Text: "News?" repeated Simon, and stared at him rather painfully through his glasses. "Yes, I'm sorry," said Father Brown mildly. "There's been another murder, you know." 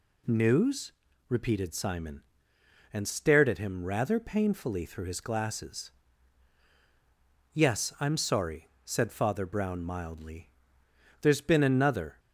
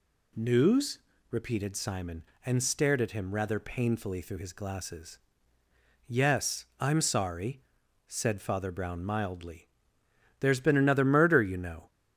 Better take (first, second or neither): second